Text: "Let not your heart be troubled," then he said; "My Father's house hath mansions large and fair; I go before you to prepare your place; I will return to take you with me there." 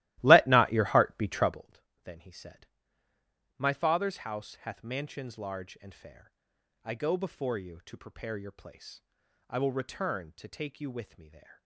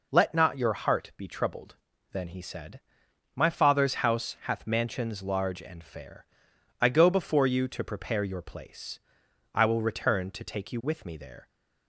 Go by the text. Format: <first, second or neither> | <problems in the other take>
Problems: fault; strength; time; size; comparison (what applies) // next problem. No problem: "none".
second | starts louder than the rest; strong; until 1.7 s; 16.5 dB